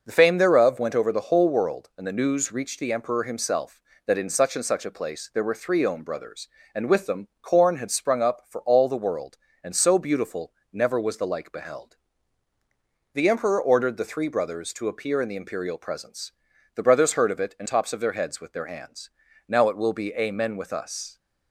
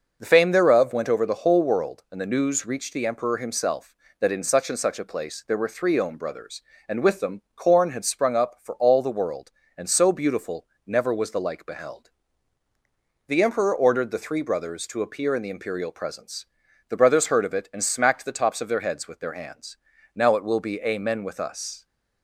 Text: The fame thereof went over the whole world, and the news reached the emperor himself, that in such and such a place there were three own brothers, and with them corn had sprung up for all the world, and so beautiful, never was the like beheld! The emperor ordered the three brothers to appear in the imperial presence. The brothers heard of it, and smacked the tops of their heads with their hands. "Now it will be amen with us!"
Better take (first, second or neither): second